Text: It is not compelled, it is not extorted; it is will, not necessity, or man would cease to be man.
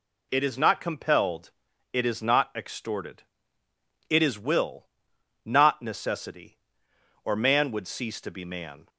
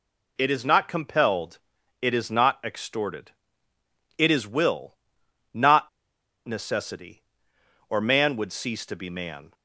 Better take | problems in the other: first | pauses between "not" and "necessity"; noticeable; at 5.8 s; 0.56 s long

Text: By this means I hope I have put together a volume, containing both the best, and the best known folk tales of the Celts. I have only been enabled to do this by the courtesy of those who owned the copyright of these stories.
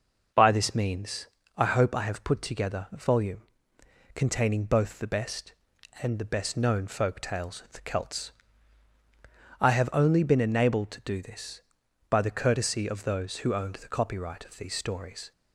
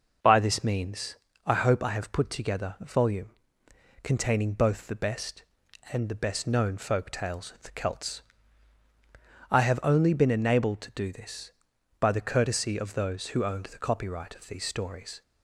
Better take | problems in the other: neither | pauses between "means" and "I"; slight; the same in both

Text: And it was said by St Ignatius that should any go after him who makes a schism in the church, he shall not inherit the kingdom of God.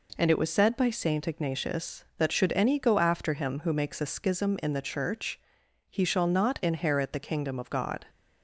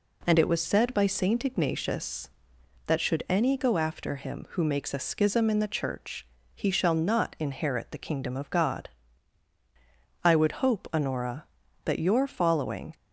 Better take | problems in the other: first | goes on to say "I would hope Honora that your following"; strong; from 10.2 s on; 2.7 s long

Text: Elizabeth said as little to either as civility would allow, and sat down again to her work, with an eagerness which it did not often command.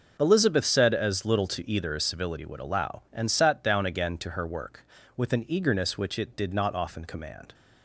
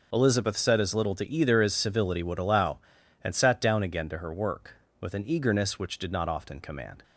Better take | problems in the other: first | skips "it"; at 5.9 s

